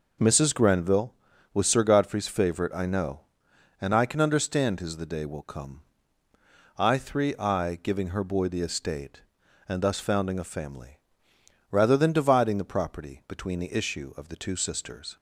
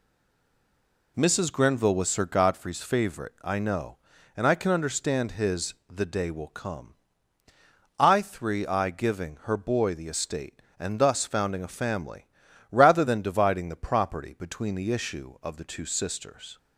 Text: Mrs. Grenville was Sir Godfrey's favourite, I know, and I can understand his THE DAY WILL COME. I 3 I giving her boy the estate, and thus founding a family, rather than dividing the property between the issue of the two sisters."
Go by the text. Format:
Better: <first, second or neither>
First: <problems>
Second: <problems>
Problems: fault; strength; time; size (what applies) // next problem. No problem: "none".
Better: first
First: none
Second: stays silent before the first word; until 1.1 s; 1.1 s long // pauses between "his" and "THE"; slight; at 5.7 s; 0.16 s long